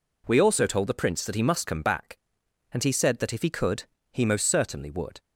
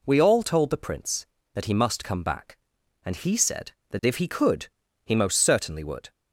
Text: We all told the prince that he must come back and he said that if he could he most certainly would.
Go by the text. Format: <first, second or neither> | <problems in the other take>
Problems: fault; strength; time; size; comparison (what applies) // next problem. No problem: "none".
second | says "also" for "all"; at 0.4 s // pauses between "could" and "he"; slight; at 3.8 s; 0.28 s long; also in the second